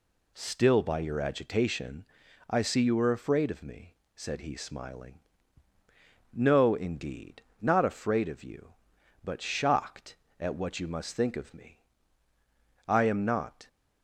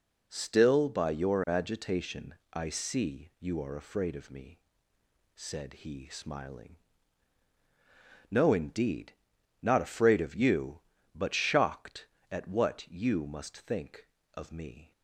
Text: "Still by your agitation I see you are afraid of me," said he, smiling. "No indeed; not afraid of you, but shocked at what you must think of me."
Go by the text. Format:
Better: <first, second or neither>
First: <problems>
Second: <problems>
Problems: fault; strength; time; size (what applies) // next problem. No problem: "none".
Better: second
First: pauses between "agitation" and "I"; at 2.0 s; 0.44 s long // goes on to say "I am not"; noticeable; from 12.8 s on; 0.80 s long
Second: pauses between "agitation" and "I"; slight; at 2.3 s; 0.18 s long